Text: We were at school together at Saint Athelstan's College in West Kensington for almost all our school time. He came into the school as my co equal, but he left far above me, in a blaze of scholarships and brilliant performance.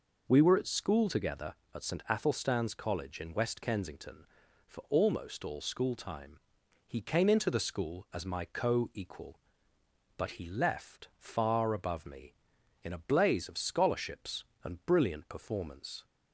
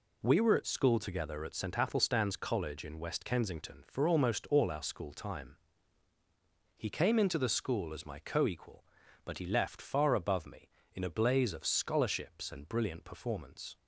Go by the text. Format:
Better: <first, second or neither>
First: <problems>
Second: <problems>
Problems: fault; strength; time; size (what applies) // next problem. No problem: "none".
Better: second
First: skips "our"; at 5.6 s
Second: none